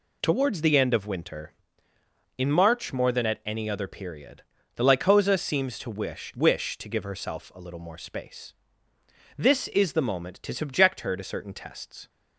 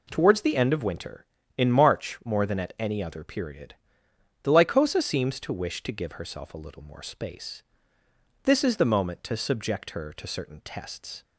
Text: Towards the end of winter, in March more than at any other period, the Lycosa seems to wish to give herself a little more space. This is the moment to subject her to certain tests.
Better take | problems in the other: second | says "wish" twice; at 6.3 s

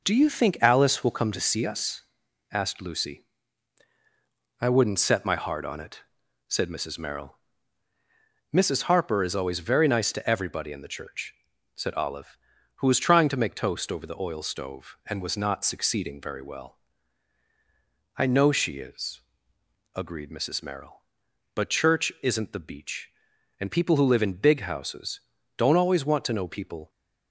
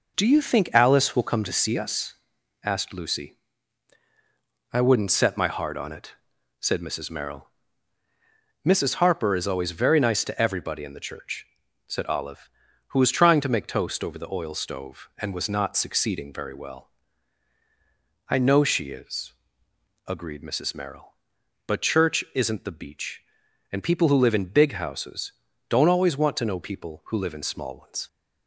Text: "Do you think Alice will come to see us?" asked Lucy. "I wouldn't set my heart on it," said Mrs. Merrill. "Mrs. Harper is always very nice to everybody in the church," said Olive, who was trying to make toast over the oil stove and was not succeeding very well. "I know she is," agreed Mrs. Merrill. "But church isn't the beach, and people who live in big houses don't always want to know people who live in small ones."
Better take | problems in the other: second | pauses between "houses" and "don't"; slight; at 25.2 s; 0.34 s long; slight in the second // stops before "who live in small ones"; at 26.8 s

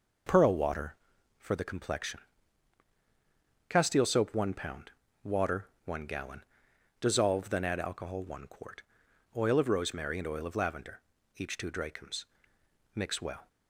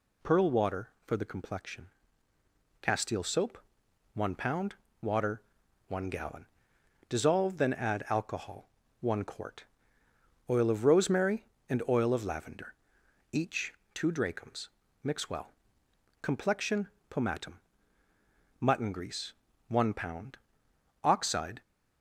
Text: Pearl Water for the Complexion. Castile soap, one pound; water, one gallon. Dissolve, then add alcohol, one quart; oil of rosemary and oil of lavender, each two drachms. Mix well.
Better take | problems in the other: first | pauses between "each" and "two"; slight; at 13.7 s; 0.22 s long // goes on to say "Complexion Pomatum Mutton grease one pound oxide"; strong; from 16.2 s on; 5.4 s long

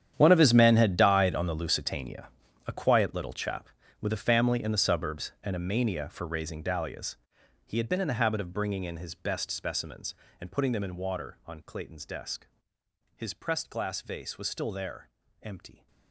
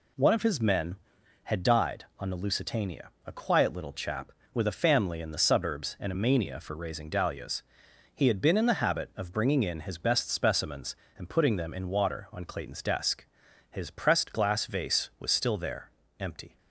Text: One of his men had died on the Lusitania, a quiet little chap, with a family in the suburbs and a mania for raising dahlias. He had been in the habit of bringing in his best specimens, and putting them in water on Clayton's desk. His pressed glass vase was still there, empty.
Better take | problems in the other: second | gets quieter; strong; throughout; 16.5 dB

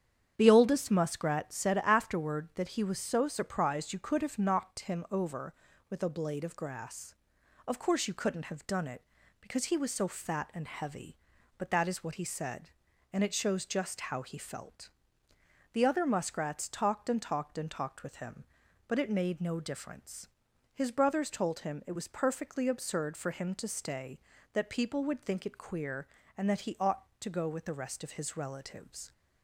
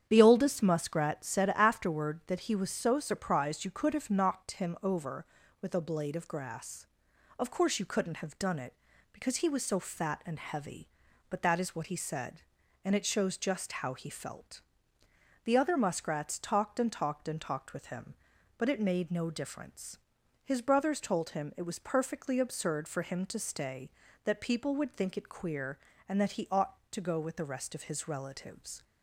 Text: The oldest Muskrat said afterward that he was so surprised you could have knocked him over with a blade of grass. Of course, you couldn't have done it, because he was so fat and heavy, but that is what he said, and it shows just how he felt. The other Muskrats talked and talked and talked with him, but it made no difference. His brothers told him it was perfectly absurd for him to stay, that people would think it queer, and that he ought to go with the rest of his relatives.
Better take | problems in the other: neither | starts louder than the rest; strong; the same in both

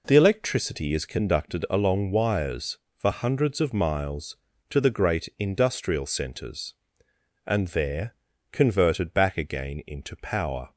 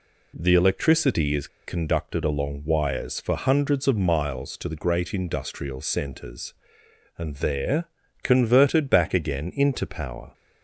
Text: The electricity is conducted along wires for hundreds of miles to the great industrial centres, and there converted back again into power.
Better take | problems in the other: first | pauses between "is" and "conducted"; slight; at 1.4 s; 0.19 s long // pauses between "there" and "converted"; slight; at 7.8 s; 0.36 s long; slight in the first

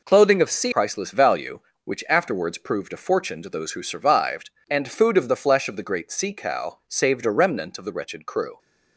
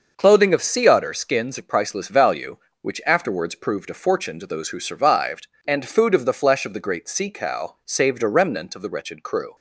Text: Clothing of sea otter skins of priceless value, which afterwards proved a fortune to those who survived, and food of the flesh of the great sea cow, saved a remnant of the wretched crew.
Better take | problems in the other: second | skips "otter skins of"; at 0.7 s

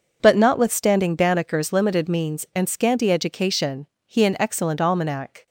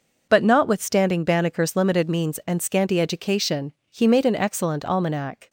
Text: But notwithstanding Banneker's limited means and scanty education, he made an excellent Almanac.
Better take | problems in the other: second | skips "made"; at 4.2 s

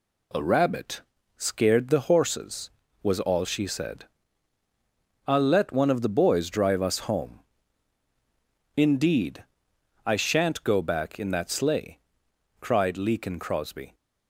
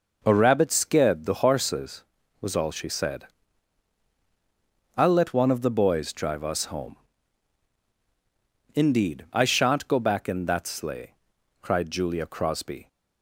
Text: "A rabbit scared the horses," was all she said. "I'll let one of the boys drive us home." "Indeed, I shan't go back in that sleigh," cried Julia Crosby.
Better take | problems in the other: second | pauses between "rabbit" and "scared"; slight; at 1.0 s; 0.34 s long // says "Leakin" for "Julia"; at 12.9 s

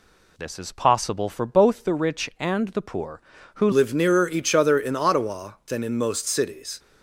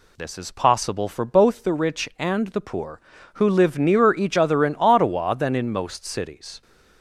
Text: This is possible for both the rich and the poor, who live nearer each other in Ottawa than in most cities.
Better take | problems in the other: second | changes voice at "live"; from 3.7 s on; 3.0 s long

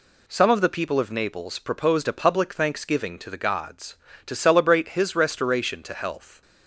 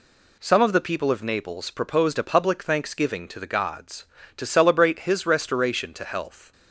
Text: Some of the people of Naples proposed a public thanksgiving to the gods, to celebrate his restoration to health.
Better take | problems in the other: neither | none

